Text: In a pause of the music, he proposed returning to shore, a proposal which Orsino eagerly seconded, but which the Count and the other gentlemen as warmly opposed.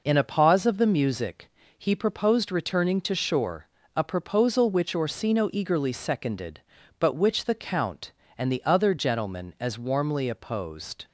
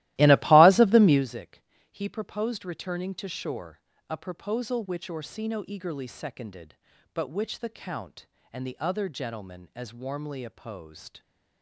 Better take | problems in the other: first | starts louder than the rest; strong; until 1.2 s; 16.5 dB

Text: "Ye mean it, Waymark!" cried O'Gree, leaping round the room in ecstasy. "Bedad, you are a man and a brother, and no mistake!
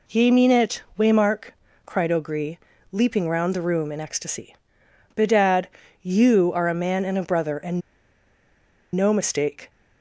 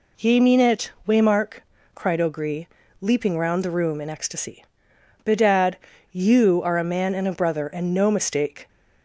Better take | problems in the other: second | pauses between "and" and "no"; at 7.8 s; 1.1 s long

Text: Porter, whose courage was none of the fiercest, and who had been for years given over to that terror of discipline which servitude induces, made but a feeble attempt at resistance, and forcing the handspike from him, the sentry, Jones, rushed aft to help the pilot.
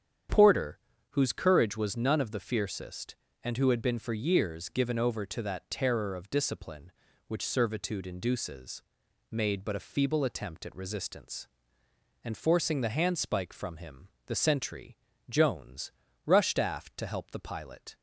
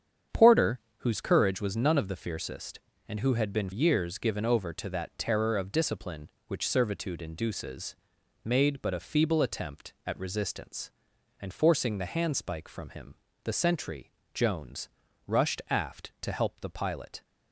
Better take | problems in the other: first | starts louder than the rest; strong; until 1.5 s; 8 dB; strong in the first // skips "for"; at 3.7 s

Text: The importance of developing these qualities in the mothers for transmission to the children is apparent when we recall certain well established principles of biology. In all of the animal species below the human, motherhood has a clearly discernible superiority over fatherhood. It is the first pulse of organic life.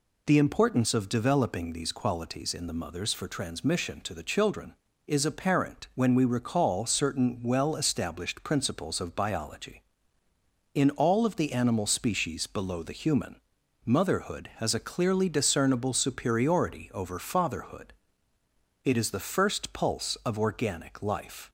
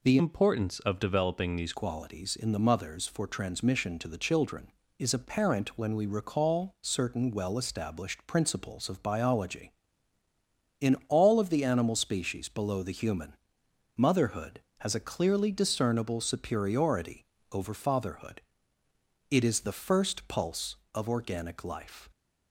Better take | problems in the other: first | changes voice from "importance" to "these"; from 0.1 to 1.7 s; 1.6 s long // pauses between "superiority" and "over"; slight; at 17.2 s; 0.28 s long

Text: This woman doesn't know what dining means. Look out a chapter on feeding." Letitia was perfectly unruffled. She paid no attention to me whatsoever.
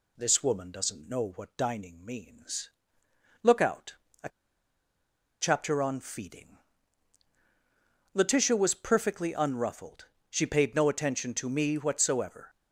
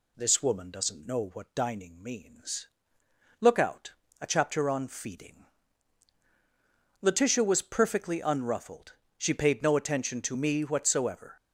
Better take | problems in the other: second | pauses between "out" and "a"; slight; at 3.9 s; 0.28 s long; slight in the second // pauses between "a" and "chapter"; at 4.2 s; 1.1 s long

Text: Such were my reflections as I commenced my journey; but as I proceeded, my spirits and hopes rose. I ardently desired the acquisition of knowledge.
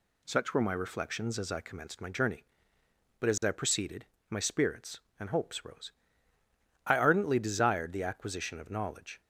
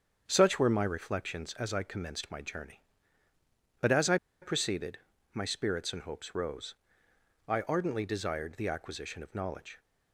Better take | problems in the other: first | starts louder than the rest; strong; until 1.2 s; 7.5 dB // pauses between "I" and "proceeded"; slight; at 4.1 s; 0.26 s long

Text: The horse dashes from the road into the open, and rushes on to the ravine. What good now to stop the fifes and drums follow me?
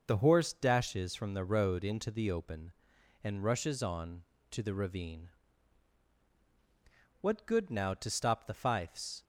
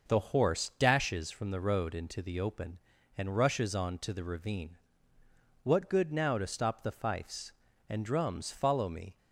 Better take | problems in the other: second | stops before "and drums follow me"; at 9.2 s

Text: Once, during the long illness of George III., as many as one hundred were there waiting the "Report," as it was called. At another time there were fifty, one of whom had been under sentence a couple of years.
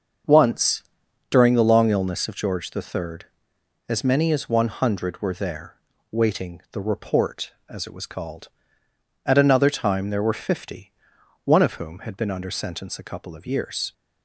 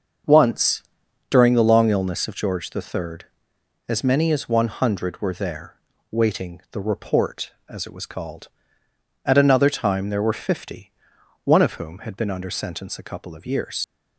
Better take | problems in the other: first | starts louder than the rest; until 1.7 s; 7 dB; also in the first // pauses between "there" and "waiting"; slight; at 5.7 s; 0.36 s long; slight in the first // leaves "years" unfinished; at 13.8 s; 80 ms

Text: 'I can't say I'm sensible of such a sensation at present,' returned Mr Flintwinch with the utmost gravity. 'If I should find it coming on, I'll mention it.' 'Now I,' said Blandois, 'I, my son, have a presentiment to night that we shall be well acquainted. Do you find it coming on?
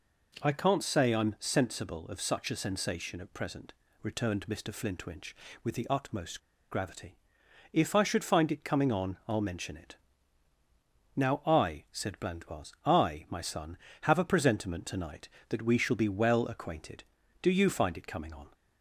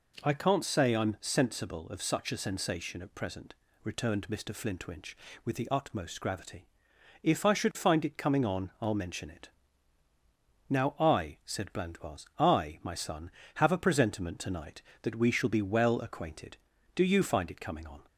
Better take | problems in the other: second | pauses between "utmost" and "gravity"; slight; at 6.3 s; 0.31 s long

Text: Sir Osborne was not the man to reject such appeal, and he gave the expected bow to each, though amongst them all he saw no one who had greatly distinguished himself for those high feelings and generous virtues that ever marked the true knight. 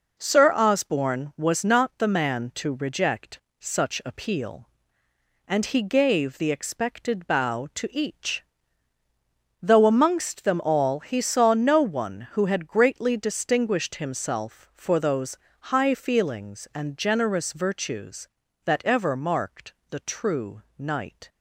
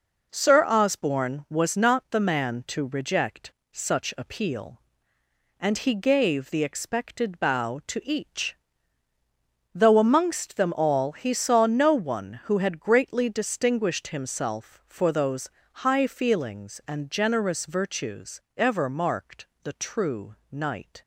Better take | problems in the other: first | pauses between "reject" and "such"; slight; at 3.5 s; 0.20 s long; slight in the first // pauses between "those" and "high"; slight; at 15.4 s; 0.22 s long; slight in the first // skips "that"; at 18.4 s // pauses between "marked" and "the"; slight; at 19.4 s; 0.16 s long; slight in the first // pauses between "true" and "knight"; slight; at 20.3 s; 0.16 s long; slight in the first

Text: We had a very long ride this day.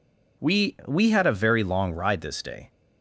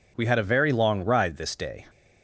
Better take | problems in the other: second | says "We" twice; at 0.8 s

